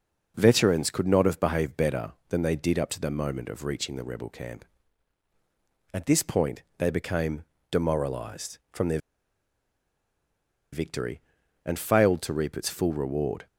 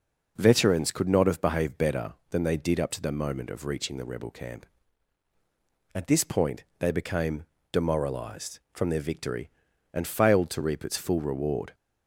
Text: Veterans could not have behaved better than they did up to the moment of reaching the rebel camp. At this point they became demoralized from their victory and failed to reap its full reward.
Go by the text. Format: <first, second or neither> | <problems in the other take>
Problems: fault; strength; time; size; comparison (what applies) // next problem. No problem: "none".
second | pauses between "point" and "they"; slight; at 6.6 s; 0.16 s long; slight in the second // pauses between "became" and "demoralized"; slight; at 7.4 s; 0.26 s long; slight in the second // pauses between "their" and "victory"; strong; at 8.9 s; 1.7 s long